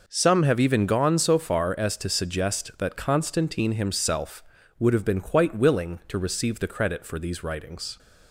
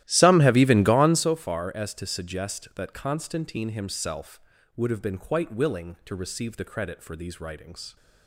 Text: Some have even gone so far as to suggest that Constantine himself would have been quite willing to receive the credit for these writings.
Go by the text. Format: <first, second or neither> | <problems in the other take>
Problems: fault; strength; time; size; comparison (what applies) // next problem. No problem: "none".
first | starts louder than the rest; strong; until 1.4 s; 14.5 dB